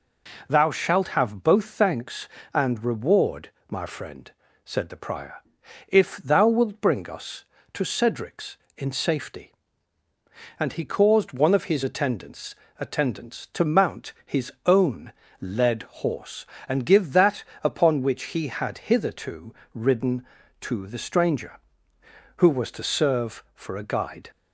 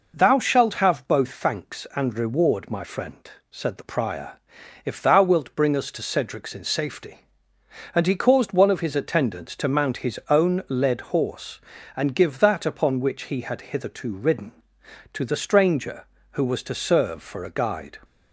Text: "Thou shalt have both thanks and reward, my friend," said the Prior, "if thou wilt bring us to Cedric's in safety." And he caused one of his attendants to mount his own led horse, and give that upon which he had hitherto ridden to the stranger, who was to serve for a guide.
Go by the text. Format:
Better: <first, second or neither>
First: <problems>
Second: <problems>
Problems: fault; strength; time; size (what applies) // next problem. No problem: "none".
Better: second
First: says "attendants" twice; at 12.7 s // pauses between "own" and "led"; slight; at 15.1 s; 0.28 s long // pauses between "led" and "horse"; slight; at 15.8 s; 0.18 s long // pauses between "that" and "upon"; slight; at 17.4 s; 0.20 s long // pauses between "hitherto" and "ridden"; slight; at 19.5 s; 0.22 s long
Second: none